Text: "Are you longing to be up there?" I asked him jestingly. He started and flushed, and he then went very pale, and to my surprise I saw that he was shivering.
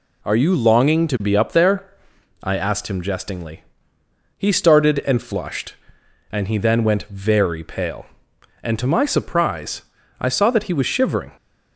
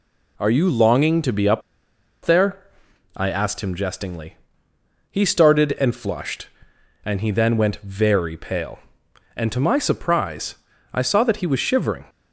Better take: first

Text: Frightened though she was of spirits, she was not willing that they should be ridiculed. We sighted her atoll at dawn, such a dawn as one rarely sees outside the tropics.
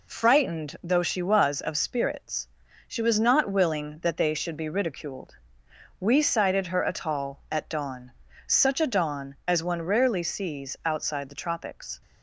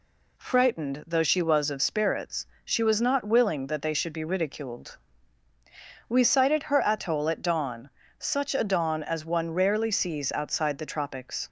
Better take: second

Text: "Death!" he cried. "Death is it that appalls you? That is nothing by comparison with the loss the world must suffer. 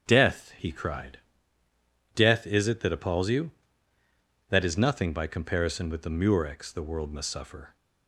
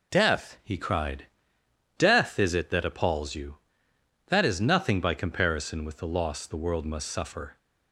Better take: second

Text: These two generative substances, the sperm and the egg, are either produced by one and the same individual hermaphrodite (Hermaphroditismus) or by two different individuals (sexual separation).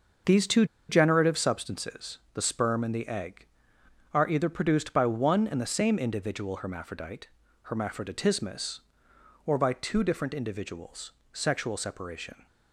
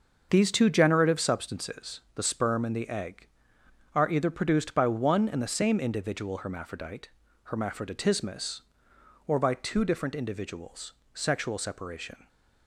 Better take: second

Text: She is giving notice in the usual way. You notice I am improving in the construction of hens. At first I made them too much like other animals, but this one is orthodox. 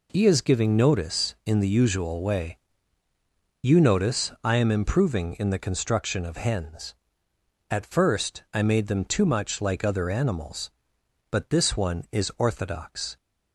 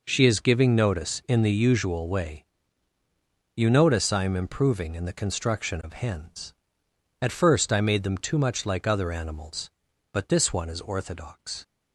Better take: second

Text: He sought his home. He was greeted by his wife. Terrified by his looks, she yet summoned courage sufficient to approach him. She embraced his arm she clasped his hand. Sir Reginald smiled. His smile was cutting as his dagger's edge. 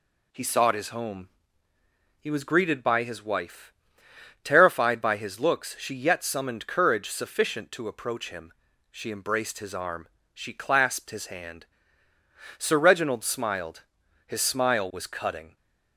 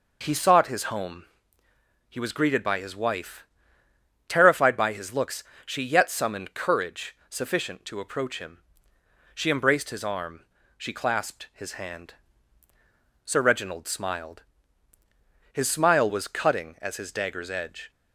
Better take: second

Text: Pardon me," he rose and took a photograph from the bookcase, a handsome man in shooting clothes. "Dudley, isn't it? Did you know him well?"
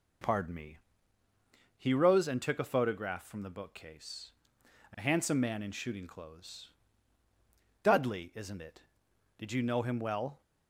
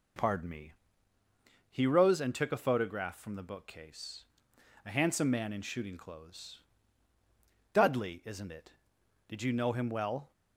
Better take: neither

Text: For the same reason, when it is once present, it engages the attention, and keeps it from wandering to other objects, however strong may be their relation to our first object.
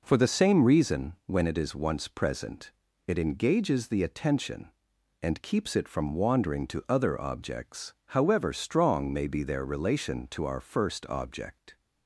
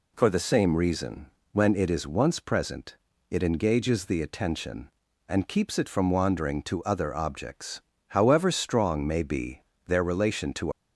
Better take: first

